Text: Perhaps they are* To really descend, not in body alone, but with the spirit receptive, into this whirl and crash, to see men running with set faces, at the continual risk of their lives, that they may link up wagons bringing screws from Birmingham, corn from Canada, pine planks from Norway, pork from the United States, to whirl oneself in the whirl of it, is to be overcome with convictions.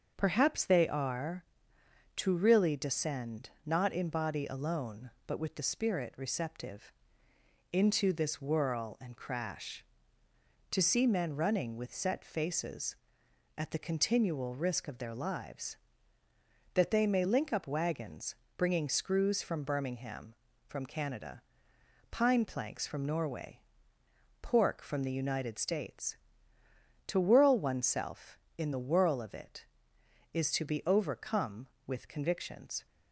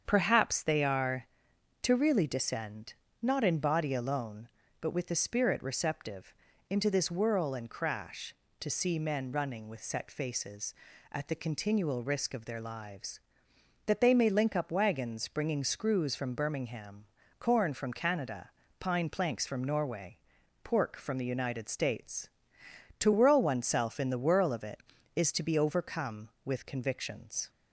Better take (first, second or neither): second